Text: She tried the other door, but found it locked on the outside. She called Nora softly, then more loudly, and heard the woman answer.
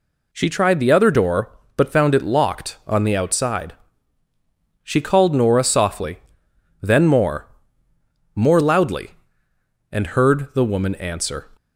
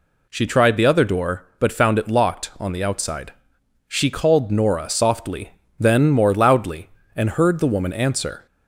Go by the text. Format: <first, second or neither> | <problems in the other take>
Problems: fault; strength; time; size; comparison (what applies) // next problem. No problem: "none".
second | says "more" twice; at 8.3 s